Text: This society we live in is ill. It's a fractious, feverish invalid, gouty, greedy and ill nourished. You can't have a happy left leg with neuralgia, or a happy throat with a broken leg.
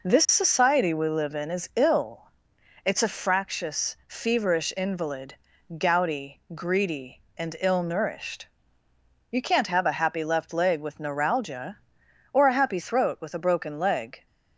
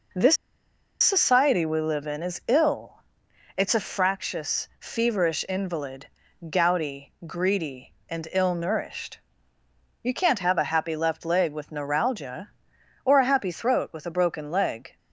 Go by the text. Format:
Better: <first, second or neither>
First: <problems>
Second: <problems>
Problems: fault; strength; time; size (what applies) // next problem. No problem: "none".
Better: first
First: none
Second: pauses between "This" and "society"; noticeable; at 0.3 s; 0.65 s long